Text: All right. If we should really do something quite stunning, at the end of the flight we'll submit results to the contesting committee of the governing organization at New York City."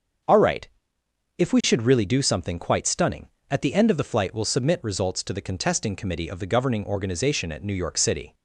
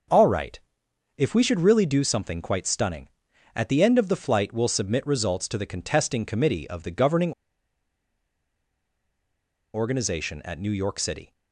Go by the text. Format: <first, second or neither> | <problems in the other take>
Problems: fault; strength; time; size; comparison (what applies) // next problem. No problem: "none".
first | starts louder than the rest; noticeable; until 1.6 s; 6 dB; also in the first // pauses between "governing" and "organization"; strong; at 7.3 s; 2.4 s long